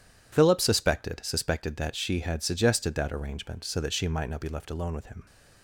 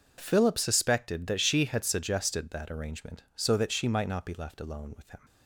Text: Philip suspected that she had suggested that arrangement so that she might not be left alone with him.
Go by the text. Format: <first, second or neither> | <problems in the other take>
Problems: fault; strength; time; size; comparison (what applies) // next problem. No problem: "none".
second | says "suspected" twice; at 1.2 s